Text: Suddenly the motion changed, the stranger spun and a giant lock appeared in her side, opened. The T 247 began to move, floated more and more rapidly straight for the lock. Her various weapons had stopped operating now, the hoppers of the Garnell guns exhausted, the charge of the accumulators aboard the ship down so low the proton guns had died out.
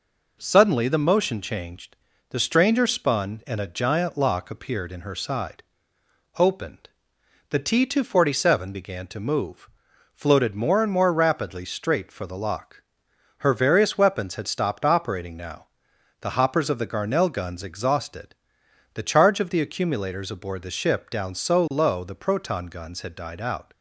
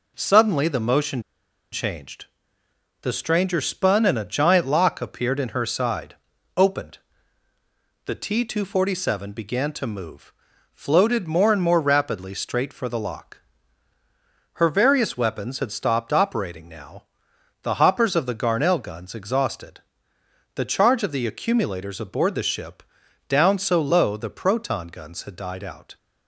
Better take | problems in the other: first | pauses between "motion" and "changed"; noticeable; at 1.2 s; 0.51 s long // pauses between "ship" and "down"; noticeable; at 22.8 s; 0.48 s long

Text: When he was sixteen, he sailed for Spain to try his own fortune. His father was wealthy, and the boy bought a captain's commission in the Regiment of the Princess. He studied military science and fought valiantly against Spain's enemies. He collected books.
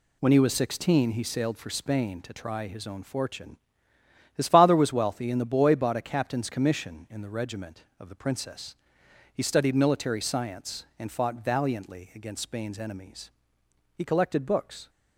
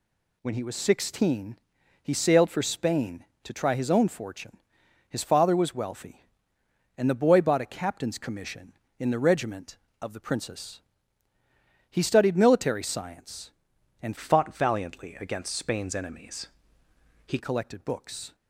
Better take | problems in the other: first | changes voice from "fought" to "He"; from 14.1 to 17.3 s; 3.2 s long

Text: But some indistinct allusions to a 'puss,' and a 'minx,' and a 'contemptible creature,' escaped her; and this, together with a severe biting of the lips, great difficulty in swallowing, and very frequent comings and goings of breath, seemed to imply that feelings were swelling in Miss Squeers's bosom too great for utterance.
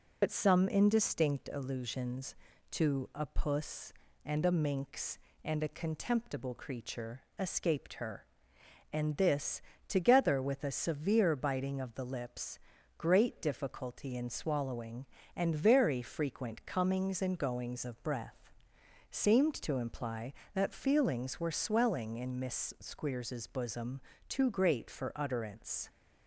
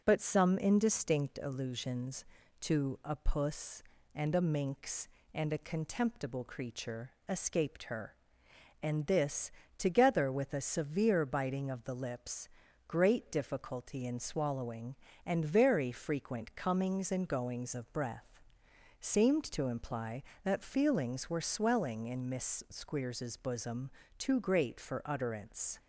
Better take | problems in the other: second | loses the start of "But"; at 0.2 s; 80 ms // pauses between "bosom" and "too"; slight; at 23.9 s; 0.30 s long; slight in the second

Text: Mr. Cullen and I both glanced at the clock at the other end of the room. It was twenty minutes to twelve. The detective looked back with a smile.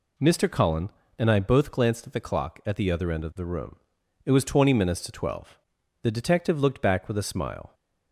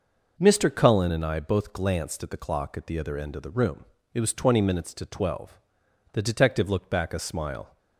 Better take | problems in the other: first | skips "with"; at 7.1 s

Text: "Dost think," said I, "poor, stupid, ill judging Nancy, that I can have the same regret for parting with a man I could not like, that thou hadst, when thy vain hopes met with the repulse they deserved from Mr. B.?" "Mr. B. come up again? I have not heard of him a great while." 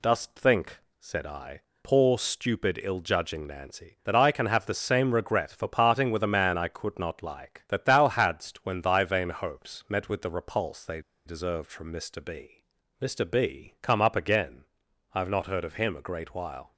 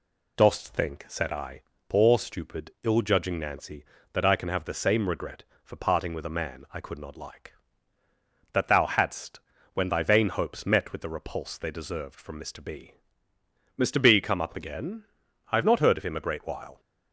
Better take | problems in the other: second | pauses between "they" and "deserved"; slight; at 11.0 s; 0.24 s long

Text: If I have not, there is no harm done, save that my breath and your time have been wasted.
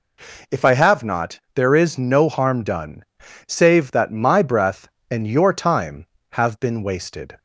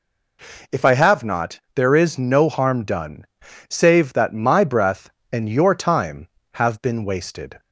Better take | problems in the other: neither | none

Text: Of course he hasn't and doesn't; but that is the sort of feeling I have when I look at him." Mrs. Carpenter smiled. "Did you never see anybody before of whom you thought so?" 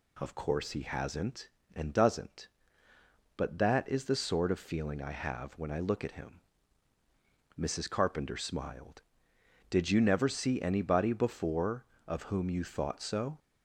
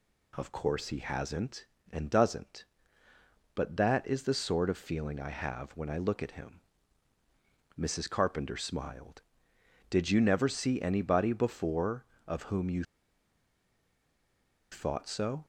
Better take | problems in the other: first | pauses between "you" and "thought"; strong; at 12.8 s; 1.8 s long

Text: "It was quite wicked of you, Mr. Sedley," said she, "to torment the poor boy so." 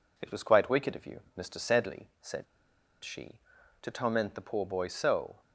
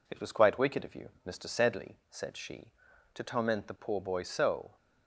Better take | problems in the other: second | pauses between "said" and "she"; noticeable; at 2.4 s; 0.59 s long

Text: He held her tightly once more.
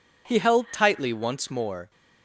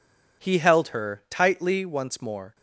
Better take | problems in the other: second | skips "her"; at 0.6 s

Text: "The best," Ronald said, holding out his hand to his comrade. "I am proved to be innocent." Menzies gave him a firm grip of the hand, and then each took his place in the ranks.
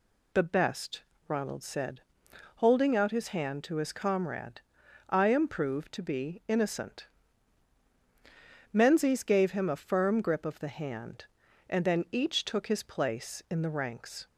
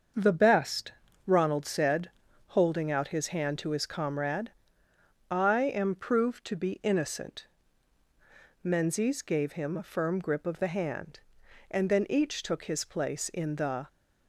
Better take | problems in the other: first | starts louder than the rest; until 1.5 s; 6.5 dB // stops before "ranks"; at 13.8 s

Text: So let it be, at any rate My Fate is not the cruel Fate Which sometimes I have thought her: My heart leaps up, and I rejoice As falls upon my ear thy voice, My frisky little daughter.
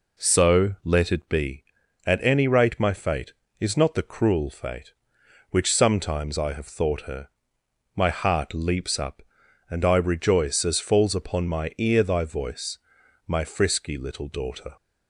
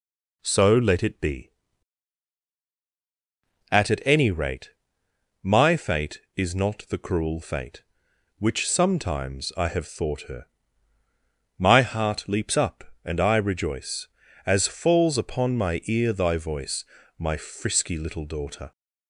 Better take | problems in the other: first | says "at" twice; at 3.8 s // pauses between "rate" and "My"; noticeable; at 4.6 s; 0.74 s long

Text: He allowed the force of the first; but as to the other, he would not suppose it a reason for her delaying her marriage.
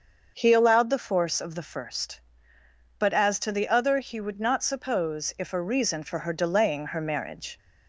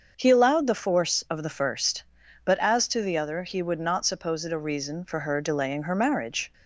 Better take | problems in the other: second | starts louder than the rest; until 1.3 s; 6.5 dB; also in the second // says "if" for "it"; at 5.3 s

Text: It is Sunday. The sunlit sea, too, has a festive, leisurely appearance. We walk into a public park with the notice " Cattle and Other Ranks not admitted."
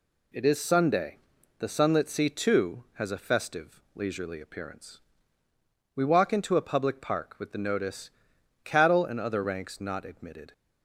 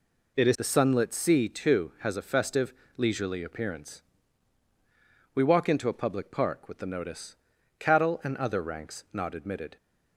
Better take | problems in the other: first | skips "Sunday"; at 0.5 s

